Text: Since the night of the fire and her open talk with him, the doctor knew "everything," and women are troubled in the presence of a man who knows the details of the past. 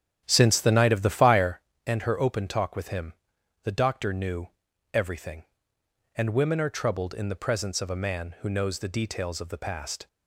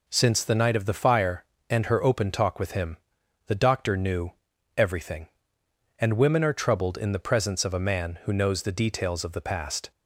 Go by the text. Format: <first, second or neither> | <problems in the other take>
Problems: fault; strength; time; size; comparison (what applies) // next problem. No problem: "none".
second | starts louder than the rest; strong; until 1.6 s; 9.5 dB // pauses between "knew" and "everything"; noticeable; at 4.4 s; 0.46 s long; noticeable in the second